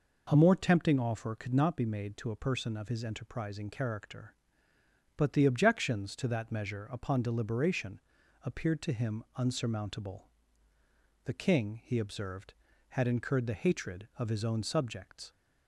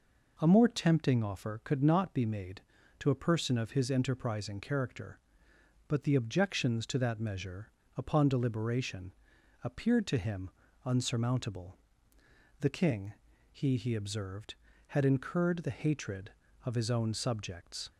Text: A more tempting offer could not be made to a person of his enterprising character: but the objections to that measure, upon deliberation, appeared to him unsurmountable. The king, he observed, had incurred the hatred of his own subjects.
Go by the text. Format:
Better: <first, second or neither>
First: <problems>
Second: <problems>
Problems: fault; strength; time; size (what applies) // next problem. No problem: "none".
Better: first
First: none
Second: pauses between "him" and "unsurmountable"; slight; at 10.5 s; 0.32 s long // says "he" twice; at 13.7 s